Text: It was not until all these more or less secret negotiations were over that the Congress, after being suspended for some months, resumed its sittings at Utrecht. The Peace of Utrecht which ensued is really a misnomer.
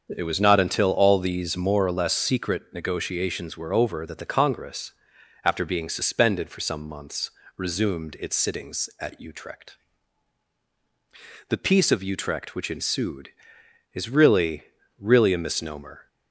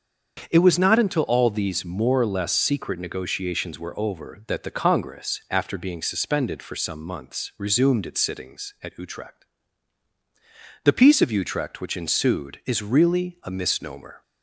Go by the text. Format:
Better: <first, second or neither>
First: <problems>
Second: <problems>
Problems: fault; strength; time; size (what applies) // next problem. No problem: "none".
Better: second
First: starts louder than the rest; until 1.1 s; 7 dB // says "really" twice; at 14.9 s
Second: starts louder than the rest; until 1.5 s; 7 dB